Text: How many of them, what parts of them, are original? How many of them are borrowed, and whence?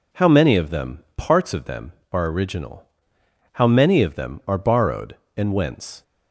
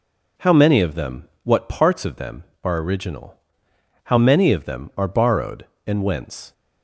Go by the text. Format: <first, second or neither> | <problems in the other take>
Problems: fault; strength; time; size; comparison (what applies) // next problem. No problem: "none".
second | skips "what"; at 1.1 s